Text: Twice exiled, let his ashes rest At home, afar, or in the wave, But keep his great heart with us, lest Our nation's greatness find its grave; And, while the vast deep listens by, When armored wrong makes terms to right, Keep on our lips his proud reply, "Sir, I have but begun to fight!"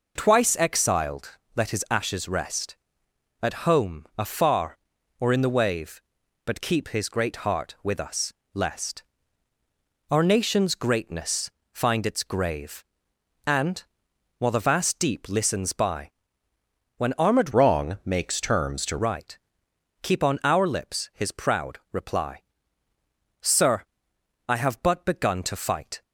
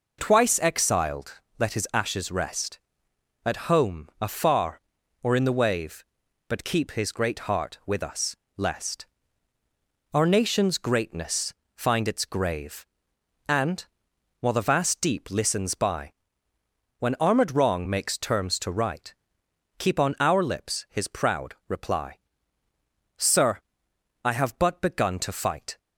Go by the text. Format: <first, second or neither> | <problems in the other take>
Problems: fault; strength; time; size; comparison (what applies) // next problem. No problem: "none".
second | pauses between "lest" and "Our"; at 9.0 s; 1.0 s long; also in the second // pauses between "greatness" and "find"; slight; at 11.5 s; 0.22 s long; slight in the second // changes voice from "wrong" to "to"; from 17.5 to 18.9 s; 1.4 s long